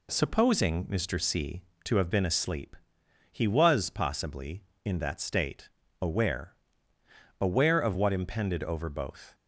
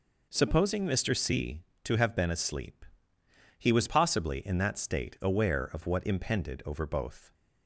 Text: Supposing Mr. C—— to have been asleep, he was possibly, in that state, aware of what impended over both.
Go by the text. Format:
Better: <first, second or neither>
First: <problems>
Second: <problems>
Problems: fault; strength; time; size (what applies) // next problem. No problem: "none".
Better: second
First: says "aware" twice; at 7.3 s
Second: none